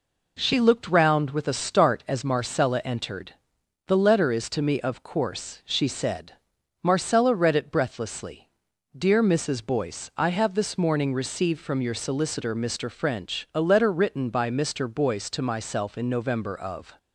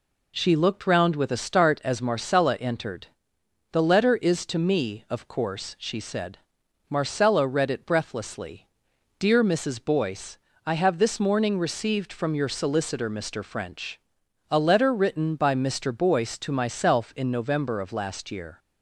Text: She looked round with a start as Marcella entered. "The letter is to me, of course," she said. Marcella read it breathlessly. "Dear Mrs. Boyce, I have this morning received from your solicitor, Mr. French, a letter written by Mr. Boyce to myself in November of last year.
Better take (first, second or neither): second